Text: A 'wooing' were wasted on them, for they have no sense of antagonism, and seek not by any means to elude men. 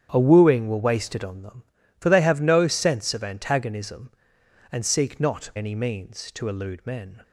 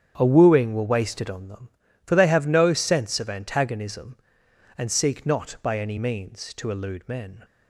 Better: second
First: starts louder than the rest; strong; until 1.1 s; 8.5 dB // skips "by"; at 5.5 s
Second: starts louder than the rest; strong; until 1.1 s; 8 dB

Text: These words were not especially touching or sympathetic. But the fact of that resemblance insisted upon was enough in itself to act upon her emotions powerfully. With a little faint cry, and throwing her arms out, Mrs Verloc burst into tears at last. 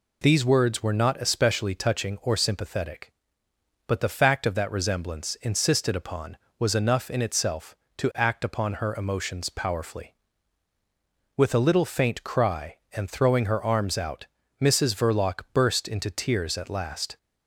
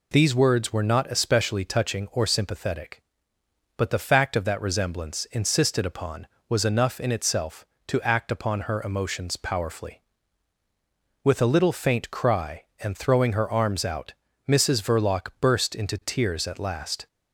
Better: neither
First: none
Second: none

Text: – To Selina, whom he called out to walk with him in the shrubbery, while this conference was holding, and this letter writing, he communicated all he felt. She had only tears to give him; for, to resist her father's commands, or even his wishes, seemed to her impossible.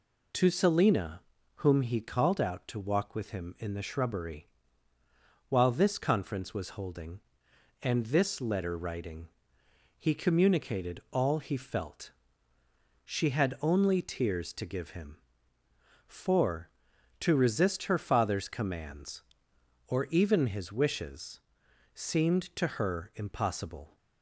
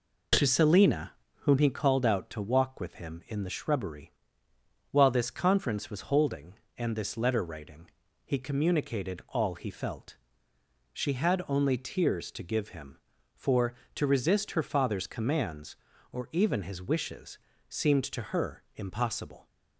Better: neither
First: none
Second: none

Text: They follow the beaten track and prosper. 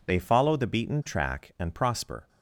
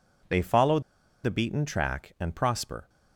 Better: first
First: none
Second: pauses between "follow" and "the"; at 0.7 s; 0.43 s long

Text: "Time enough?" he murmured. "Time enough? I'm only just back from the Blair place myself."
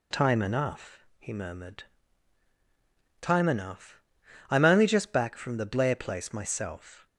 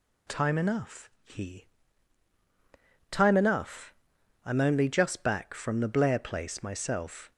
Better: first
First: none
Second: skips "murmured"; at 2.3 s

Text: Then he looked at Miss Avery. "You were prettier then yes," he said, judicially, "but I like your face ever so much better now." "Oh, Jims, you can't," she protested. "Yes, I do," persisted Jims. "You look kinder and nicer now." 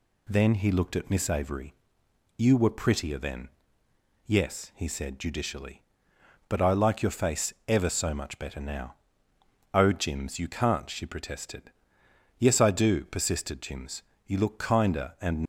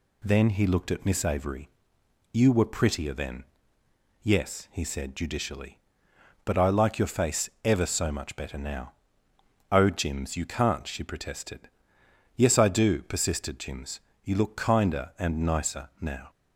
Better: second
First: pauses between "then" and "yes"; noticeable; at 3.4 s; 0.78 s long // stops before "nicer now"; at 15.4 s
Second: pauses between "then" and "yes"; noticeable; at 3.4 s; 0.79 s long

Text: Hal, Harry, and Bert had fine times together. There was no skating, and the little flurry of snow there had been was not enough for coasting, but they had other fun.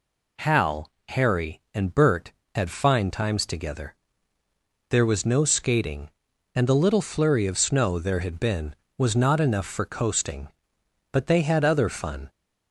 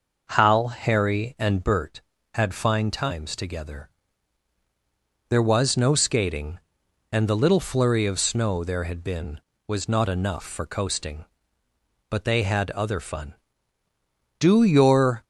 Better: first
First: none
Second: goes on to say "Do your"; noticeable; from 14.3 s on; 0.86 s long

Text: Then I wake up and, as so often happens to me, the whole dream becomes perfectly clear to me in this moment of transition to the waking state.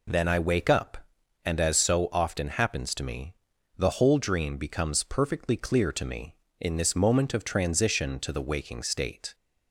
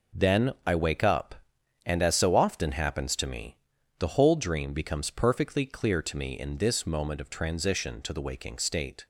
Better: first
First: none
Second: gets quieter; strong; throughout; 9.5 dB

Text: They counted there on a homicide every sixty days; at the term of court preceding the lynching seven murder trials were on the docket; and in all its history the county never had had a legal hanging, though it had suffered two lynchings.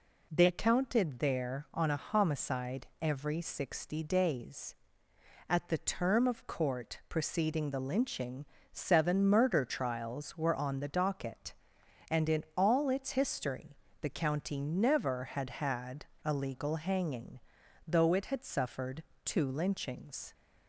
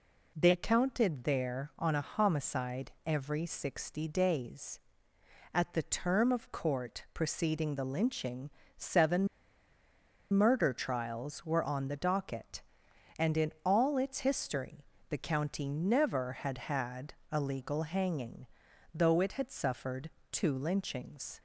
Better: first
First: pauses between "homicide" and "every"; slight; at 2.8 s; 0.16 s long // pauses between "lynching" and "seven"; slight; at 8.4 s; 0.26 s long // pauses between "history" and "the"; slight; at 13.7 s; 0.26 s long // pauses between "had" and "a"; slight; at 16.0 s; 0.17 s long // pauses between "suffered" and "two"; slight; at 19.0 s; 0.22 s long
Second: pauses between "homicide" and "every"; slight; at 2.9 s; 0.16 s long // pauses between "lynching" and "seven"; slight; at 8.5 s; 0.26 s long // pauses between "seven" and "murder"; at 9.2 s; 1.0 s long // pauses between "history" and "the"; slight; at 14.8 s; 0.26 s long // pauses between "had" and "a"; slight; at 17.1 s; 0.16 s long // pauses between "suffered" and "two"; slight; at 20.0 s; 0.22 s long

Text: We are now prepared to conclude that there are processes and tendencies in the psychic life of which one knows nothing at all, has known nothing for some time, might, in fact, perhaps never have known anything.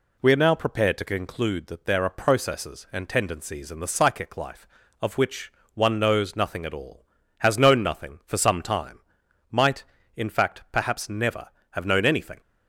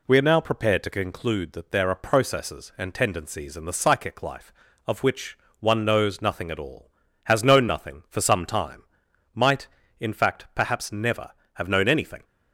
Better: neither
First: pauses between "which" and "one"; slight; at 5.5 s; 0.24 s long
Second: pauses between "which" and "one"; slight; at 5.3 s; 0.24 s long

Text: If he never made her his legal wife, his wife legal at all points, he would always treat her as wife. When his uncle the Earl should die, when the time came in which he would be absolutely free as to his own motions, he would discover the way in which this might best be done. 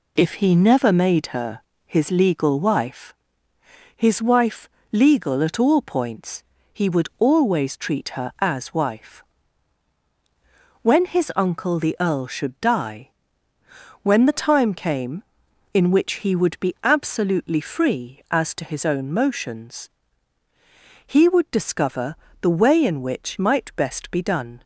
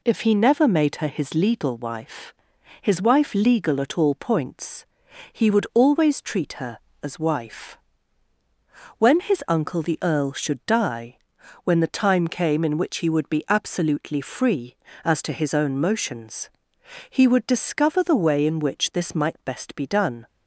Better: second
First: pauses between "her" and "his"; slight; at 1.6 s; 0.24 s long // pauses between "wife" and "legal"; slight; at 4.6 s; 0.24 s long // pauses between "discover" and "the"; slight; at 22.1 s; 0.26 s long // skips "this"; at 23.3 s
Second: none

